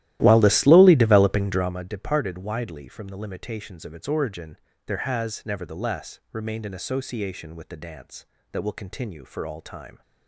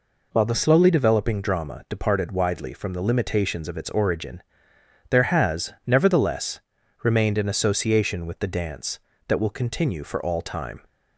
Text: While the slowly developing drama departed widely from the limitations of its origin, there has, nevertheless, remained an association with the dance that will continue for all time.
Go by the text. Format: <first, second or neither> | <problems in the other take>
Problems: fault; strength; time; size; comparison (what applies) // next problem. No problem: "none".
second | starts louder than the rest; strong; until 1.8 s; 14.5 dB